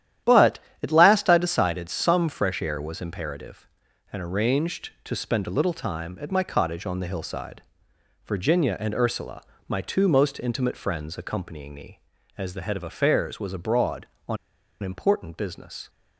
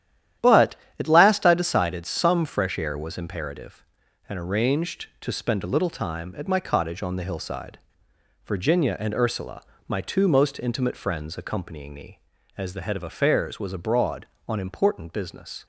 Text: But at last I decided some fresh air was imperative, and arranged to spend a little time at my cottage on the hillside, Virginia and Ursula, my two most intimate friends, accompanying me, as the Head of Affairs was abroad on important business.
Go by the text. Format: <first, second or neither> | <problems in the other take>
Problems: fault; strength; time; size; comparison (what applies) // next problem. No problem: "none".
second | starts louder than the rest; strong; until 1.4 s; 11.5 dB; strong in the second // pauses between "on" and "important"; noticeable; at 14.3 s; 0.46 s long